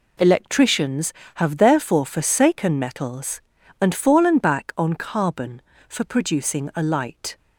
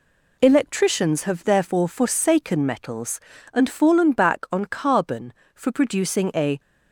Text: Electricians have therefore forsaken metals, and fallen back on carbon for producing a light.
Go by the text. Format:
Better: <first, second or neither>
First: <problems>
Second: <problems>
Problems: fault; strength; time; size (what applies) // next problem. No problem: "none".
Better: first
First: none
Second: stops before "light"; at 6.5 s